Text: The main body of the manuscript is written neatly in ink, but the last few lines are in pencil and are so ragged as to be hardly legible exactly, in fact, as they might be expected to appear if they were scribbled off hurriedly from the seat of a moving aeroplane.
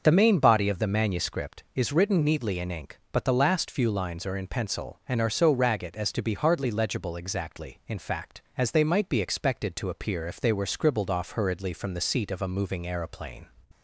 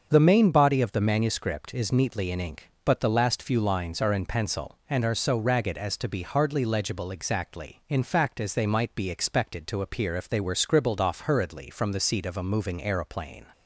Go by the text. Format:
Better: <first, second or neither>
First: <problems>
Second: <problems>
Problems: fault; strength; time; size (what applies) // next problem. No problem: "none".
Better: first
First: starts louder than the rest; until 1.0 s; 6.5 dB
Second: starts louder than the rest; until 1.1 s; 7 dB // skips "written"; at 1.9 s